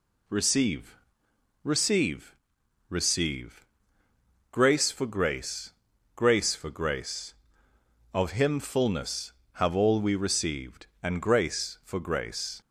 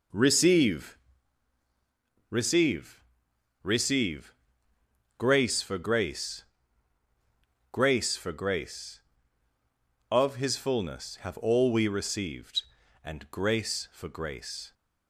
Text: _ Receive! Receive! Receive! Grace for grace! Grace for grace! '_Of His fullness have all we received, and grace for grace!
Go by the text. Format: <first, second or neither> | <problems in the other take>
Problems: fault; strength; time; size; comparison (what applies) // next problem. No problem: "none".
second | says "Him" for "His"; at 8.3 s